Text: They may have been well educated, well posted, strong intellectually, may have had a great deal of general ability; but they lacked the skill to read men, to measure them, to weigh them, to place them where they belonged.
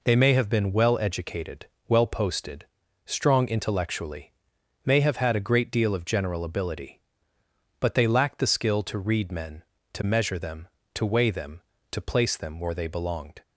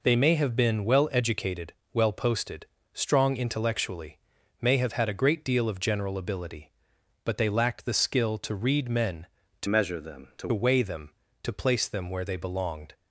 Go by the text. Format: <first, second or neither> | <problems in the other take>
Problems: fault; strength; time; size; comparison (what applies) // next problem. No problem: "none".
first | changes voice from "measure" to "to"; from 9.6 to 10.4 s; 0.8 s long